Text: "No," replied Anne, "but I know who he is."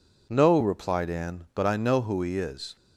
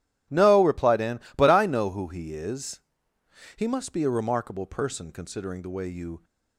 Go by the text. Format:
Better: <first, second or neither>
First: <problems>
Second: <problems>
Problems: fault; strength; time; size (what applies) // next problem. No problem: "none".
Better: first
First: none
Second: goes on to say "He must be a remarkable person considering the way you"; strong; from 3.5 s on; 2.6 s long